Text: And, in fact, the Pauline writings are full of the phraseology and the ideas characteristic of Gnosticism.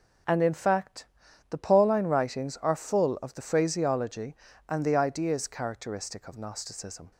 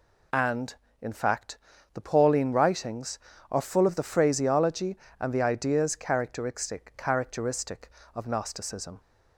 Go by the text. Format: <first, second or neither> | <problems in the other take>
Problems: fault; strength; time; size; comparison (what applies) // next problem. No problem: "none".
first | says "characteristic" twice; at 6.9 s